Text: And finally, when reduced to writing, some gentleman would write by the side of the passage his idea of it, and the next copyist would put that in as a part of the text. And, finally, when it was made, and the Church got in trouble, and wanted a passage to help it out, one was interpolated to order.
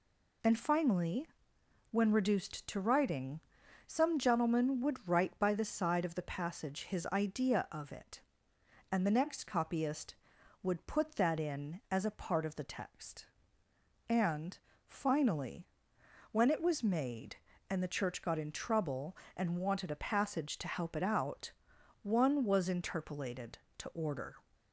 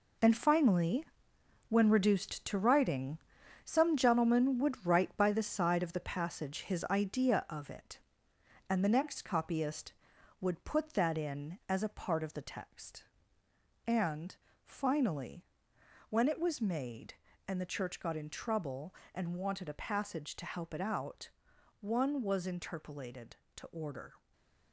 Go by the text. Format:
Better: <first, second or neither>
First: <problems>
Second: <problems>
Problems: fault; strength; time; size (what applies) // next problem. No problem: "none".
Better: first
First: none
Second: gets quieter; strong; throughout; 8.5 dB // stays silent after the last word; slight; from 24.1 s on; 0.6 s long